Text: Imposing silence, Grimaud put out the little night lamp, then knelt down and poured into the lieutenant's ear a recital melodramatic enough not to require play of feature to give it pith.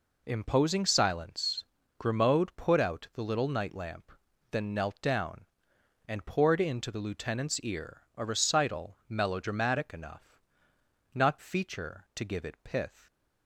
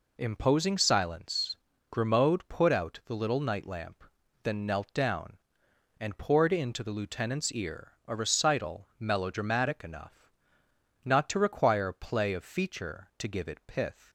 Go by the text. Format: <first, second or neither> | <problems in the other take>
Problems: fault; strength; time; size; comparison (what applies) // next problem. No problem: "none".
second | pauses between "enough" and "not"; noticeable; at 10.3 s; 0.76 s long; noticeable in the second // skips "to require play of"; at 11.3 s